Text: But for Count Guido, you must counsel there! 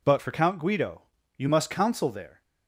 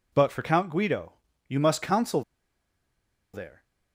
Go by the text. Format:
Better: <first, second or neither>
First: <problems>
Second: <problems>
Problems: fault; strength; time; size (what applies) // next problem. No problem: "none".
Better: first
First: none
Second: pauses between "counsel" and "there"; at 2.2 s; 1.1 s long